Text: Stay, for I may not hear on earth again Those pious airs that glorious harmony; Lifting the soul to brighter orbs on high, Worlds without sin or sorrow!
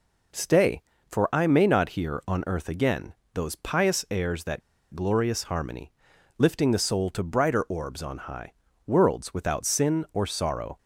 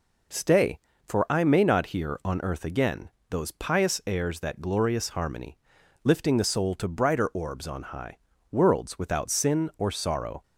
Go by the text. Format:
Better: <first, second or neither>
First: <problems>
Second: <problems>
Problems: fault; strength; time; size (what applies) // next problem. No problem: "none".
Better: second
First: pauses between "again" and "Those"; slight; at 3.1 s; 0.20 s long // pauses between "that" and "glorious"; slight; at 4.6 s; 0.32 s long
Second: pauses between "again" and "Those"; slight; at 3.0 s; 0.20 s long